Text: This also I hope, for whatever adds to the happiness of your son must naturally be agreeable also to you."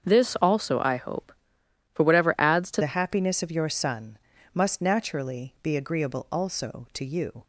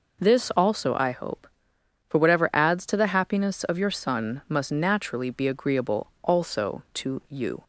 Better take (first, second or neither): second